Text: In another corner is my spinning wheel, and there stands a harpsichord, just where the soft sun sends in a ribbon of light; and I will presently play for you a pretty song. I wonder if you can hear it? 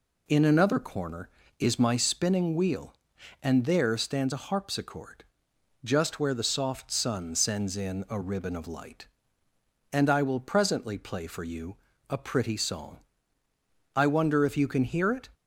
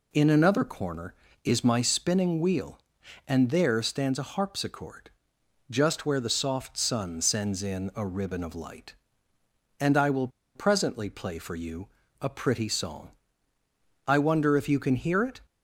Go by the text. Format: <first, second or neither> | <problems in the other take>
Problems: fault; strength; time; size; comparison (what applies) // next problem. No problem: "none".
first | pauses between "will" and "presently"; slight; at 10.2 s; 0.27 s long // pauses between "you" and "a"; slight; at 11.8 s; 0.32 s long; slight in the first